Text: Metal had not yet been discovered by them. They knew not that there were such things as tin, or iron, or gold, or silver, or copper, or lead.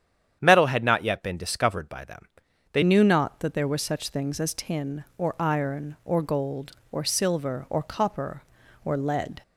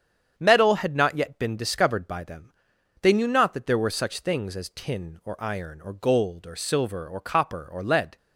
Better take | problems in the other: second | starts louder than the rest; strong; until 1.4 s; 9 dB; strong in the second // changes voice at "knew"; from 2.8 s on; 6.6 s long

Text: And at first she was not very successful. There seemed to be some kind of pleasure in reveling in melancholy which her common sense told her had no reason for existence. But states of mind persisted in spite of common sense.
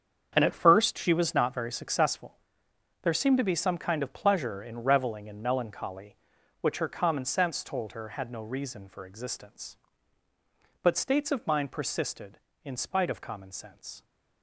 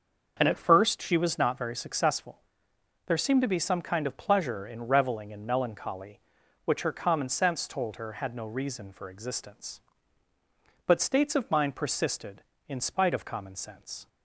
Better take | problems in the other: second | gets quieter; strong; throughout; 12 dB // starts louder than the rest; strong; until 1.3 s; 7.5 dB; also in the second

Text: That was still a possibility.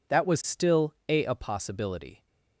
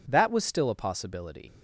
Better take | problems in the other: second | says "a" twice; at 1.2 s

